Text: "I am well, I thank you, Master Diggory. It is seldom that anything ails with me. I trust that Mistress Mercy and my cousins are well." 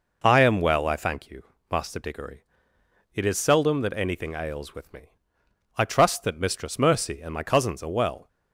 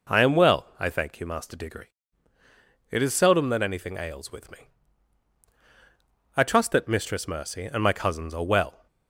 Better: neither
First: none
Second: none

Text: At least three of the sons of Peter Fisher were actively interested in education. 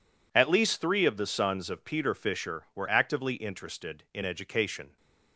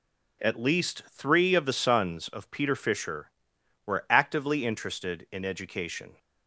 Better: neither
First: none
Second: none

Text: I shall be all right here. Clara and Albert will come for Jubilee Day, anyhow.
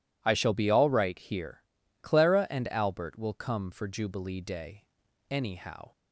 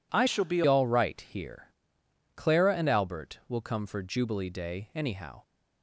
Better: first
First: none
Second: changes voice from "shall" to "be"; from 0.2 to 0.6 s; 0.4 s long

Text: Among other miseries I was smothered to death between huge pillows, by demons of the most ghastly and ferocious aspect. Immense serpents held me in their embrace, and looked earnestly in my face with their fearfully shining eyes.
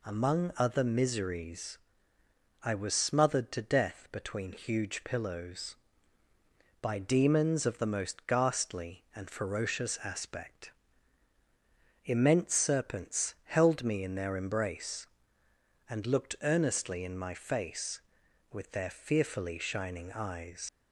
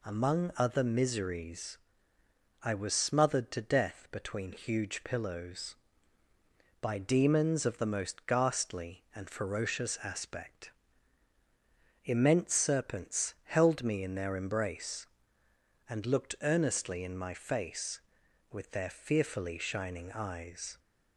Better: second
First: pauses between "miseries" and "I"; noticeable; at 1.7 s; 0.86 s long // leaves "eyes" unfinished; at 20.6 s; 100 ms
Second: pauses between "miseries" and "I"; noticeable; at 1.7 s; 0.86 s long

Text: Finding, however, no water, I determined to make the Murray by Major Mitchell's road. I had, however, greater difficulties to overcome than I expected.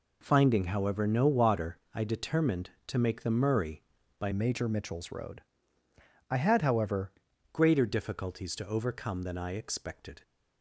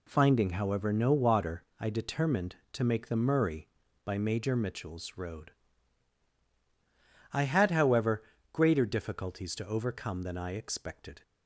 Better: second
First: changes voice from "Major" to "however"; from 4.3 to 7.1 s; 2.8 s long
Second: none

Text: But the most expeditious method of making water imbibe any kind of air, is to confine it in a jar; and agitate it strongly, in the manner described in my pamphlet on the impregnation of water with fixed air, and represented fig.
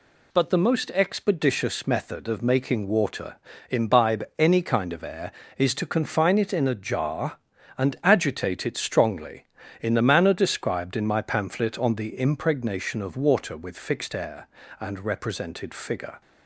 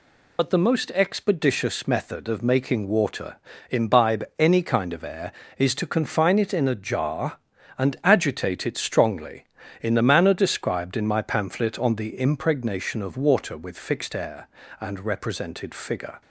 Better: first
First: pauses between "water" and "imbibe"; slight; at 3.3 s; 0.34 s long // pauses between "imbibe" and "any"; slight; at 4.2 s; 0.16 s long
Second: loses the start of "But"; at 0.3 s; 65 ms // pauses between "water" and "imbibe"; slight; at 3.3 s; 0.34 s long // pauses between "imbibe" and "any"; slight; at 4.2 s; 0.16 s long

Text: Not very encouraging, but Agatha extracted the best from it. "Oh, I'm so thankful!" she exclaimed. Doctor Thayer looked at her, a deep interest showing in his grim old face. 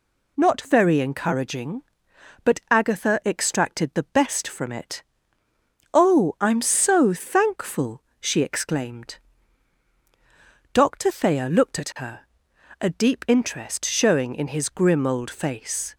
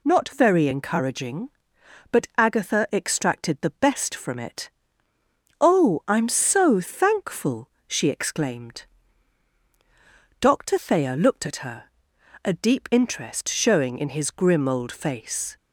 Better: neither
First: none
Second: none

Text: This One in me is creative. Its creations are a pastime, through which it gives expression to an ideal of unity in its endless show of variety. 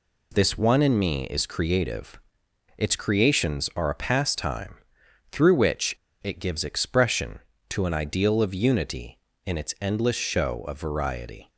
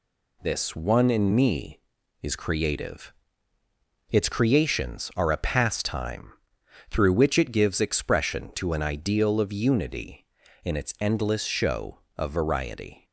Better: second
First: pauses between "which" and "it"; slight; at 5.9 s; 0.29 s long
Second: none

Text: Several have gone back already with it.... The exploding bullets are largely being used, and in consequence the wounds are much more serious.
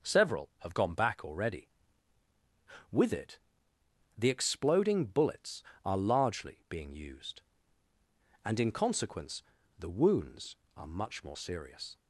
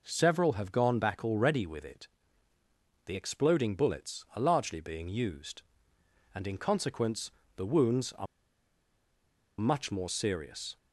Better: first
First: pauses between "consequence" and "the"; slight; at 9.4 s; 0.34 s long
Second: pauses between "consequence" and "the"; slight; at 7.3 s; 0.26 s long // pauses between "are" and "much"; strong; at 8.2 s; 1.3 s long

